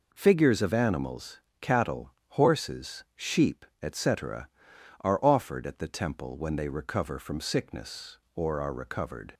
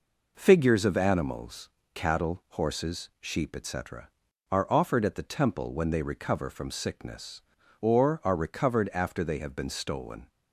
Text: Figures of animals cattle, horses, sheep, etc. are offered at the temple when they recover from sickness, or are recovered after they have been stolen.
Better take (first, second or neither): second